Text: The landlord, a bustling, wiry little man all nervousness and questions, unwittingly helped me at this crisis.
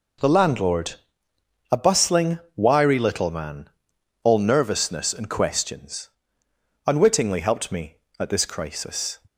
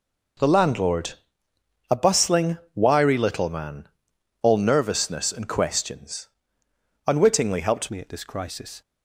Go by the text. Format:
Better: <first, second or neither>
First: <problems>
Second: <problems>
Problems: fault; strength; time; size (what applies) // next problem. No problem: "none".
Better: first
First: pauses between "man" and "all"; noticeable; at 3.6 s; 0.52 s long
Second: pauses between "man" and "all"; noticeable; at 3.8 s; 0.52 s long // changes voice at "me"; from 7.9 s on; 0.9 s long